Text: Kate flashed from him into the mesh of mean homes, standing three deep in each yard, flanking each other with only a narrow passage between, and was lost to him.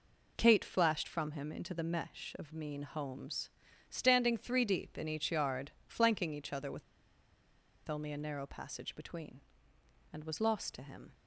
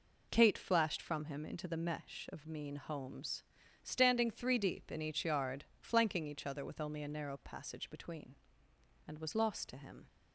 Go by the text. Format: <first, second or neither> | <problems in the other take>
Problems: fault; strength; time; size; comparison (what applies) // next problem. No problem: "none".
second | pauses between "with" and "only"; at 6.8 s; 1.0 s long